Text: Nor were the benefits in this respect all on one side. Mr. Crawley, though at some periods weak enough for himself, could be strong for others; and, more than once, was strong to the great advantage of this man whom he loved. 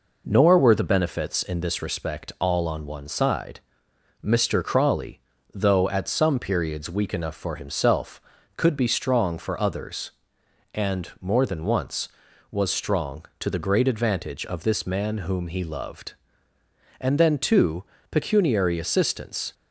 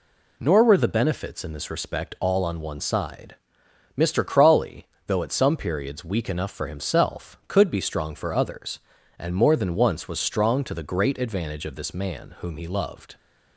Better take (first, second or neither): second